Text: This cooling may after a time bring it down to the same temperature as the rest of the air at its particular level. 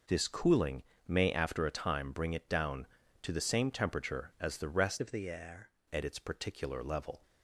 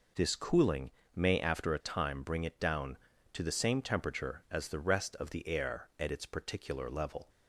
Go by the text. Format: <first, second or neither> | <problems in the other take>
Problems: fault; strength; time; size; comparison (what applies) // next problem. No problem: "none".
second | pauses between "cooling" and "may"; slight; at 0.8 s; 0.24 s long; slight in the second // changes voice from "of" to "air"; from 5.0 to 5.7 s; 0.7 s long